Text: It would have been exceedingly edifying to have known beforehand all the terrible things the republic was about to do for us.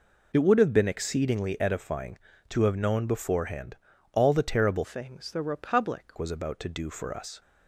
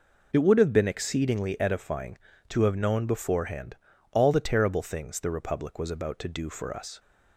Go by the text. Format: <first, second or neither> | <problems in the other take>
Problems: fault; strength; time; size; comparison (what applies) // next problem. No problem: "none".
second | pauses between "beforehand" and "all"; slight; at 3.7 s; 0.36 s long; slight in the second // changes voice from "things" to "republic"; from 4.8 to 6.1 s; 1.3 s long